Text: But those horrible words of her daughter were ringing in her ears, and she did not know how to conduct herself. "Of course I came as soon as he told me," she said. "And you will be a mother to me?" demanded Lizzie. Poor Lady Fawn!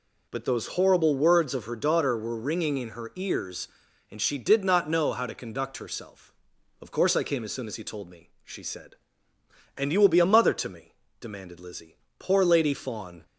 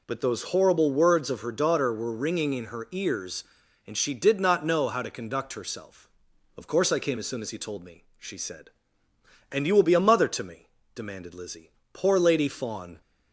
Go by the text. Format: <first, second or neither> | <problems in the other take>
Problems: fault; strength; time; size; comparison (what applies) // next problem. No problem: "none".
neither | none